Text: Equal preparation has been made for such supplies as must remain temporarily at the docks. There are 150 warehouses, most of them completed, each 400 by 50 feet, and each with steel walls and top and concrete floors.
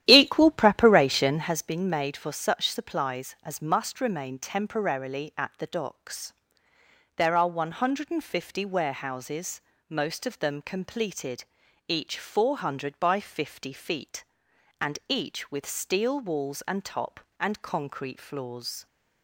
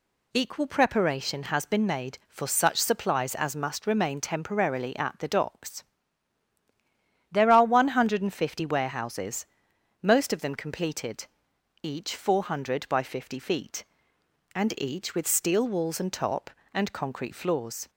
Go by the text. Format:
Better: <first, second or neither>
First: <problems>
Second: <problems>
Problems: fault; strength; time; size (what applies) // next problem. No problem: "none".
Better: second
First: starts louder than the rest; strong; until 1.5 s; 11.5 dB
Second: none